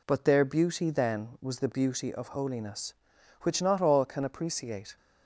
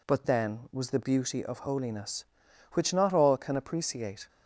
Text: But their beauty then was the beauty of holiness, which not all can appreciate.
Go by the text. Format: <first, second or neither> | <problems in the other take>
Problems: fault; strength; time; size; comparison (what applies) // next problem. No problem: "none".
first | skips "their beauty"; at 0.2 s